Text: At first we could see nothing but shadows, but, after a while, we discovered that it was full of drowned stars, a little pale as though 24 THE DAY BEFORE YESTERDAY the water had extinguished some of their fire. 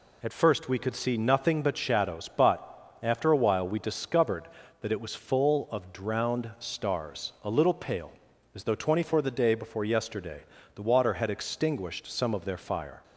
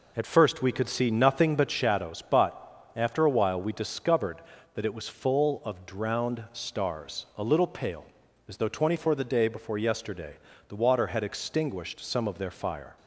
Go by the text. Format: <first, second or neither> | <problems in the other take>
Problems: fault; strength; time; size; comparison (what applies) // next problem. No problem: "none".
first | starts louder than the rest; noticeable; until 2.0 s; 4 dB // pauses between "YESTERDAY" and "the"; slight; at 10.3 s; 0.34 s long; slight in the first